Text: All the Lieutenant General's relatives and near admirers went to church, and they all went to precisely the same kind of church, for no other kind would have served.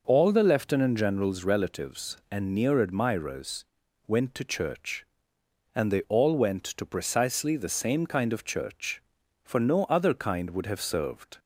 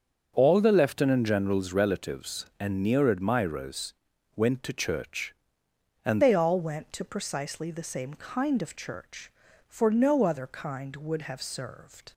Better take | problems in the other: first | starts louder than the rest; until 1.3 s; 6.5 dB // pauses between "admirers" and "went"; at 3.9 s; 0.42 s long; also in the first // changes voice at "they"; from 6.2 s on; 5.9 s long

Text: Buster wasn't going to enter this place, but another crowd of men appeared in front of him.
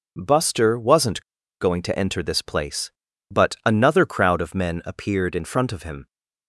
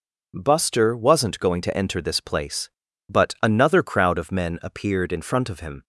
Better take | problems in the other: second | pauses between "wasn't" and "going"; at 1.2 s; 0.39 s long

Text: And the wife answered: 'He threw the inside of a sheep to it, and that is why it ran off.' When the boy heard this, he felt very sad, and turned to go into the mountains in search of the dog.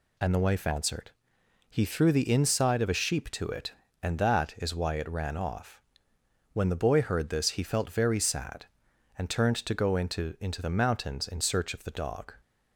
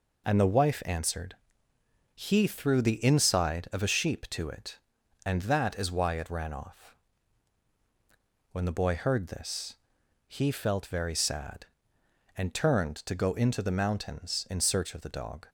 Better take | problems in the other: second | says "into" twice; at 10.3 s

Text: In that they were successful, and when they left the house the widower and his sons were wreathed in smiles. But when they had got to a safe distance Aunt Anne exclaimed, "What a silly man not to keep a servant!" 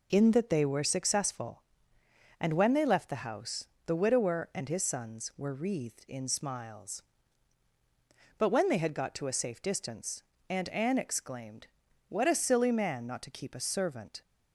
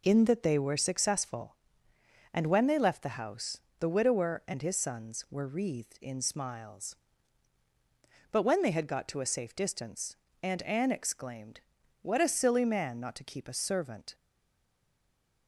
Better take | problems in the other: first | pauses between "house" and "the"; slight; at 3.6 s; 0.18 s long; slight in the first // pauses between "distance" and "Aunt"; slight; at 10.1 s; 0.28 s long; slight in the first // stays silent after the last word; noticeable; from 14.1 s on; 1.3 s long

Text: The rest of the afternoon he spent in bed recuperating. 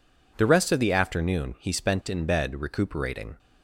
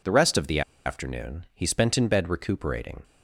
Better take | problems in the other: first | pauses between "the" and "afternoon"; slight; at 0.6 s; 0.25 s long

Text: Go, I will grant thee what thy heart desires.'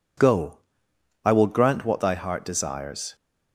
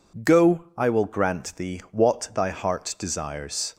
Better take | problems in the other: second | skips "thee"; at 1.8 s

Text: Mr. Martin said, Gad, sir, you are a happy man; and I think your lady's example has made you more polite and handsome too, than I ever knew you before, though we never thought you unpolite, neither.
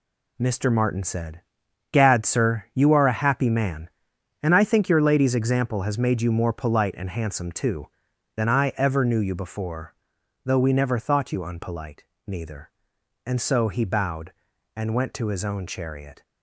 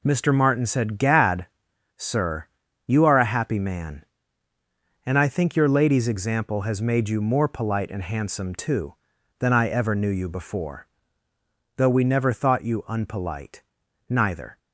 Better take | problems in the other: second | goes on to say "And so he bowed and went to his own chariot"; strong; from 13.2 s on; 2.9 s long

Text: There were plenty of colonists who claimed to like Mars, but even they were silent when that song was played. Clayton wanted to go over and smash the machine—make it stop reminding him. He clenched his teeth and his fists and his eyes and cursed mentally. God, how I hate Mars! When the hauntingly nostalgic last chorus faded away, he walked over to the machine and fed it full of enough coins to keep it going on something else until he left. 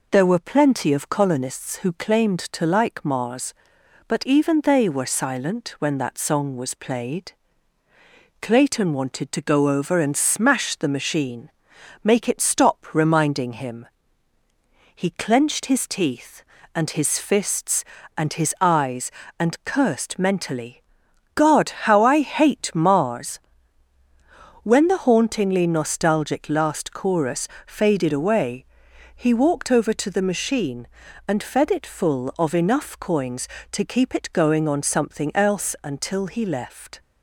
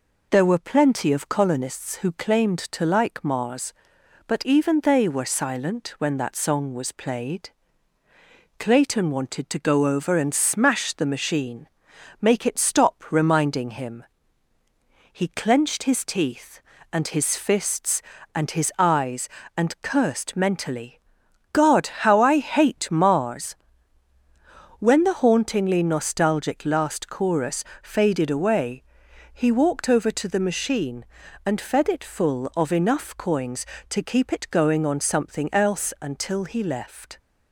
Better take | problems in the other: neither | pauses between "chorus" and "faded"; slight; the same in both

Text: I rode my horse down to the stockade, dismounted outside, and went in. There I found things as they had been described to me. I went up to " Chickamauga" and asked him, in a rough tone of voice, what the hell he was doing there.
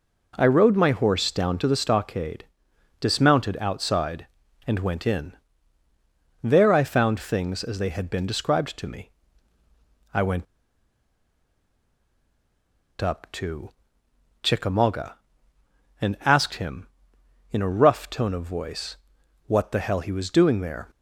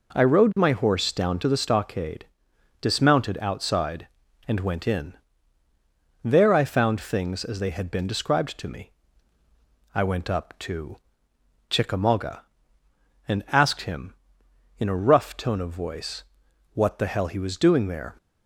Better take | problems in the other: second | pauses between "went" and "up"; strong; at 10.4 s; 2.5 s long

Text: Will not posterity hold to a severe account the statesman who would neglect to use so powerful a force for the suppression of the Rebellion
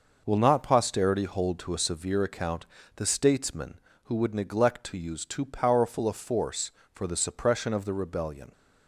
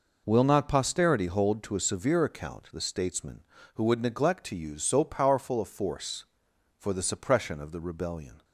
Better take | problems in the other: second | pauses between "account" and "the"; slight; at 2.6 s; 0.30 s long // says "too" for "so"; at 5.2 s

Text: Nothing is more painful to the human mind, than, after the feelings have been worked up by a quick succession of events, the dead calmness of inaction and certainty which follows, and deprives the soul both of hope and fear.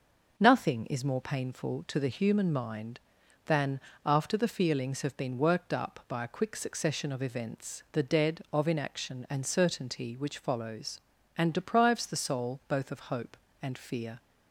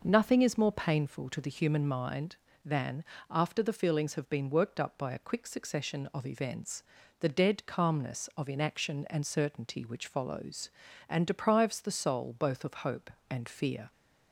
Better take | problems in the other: second | starts louder than the rest; until 1.4 s; 6 dB // skips "calmness"; at 8.4 s

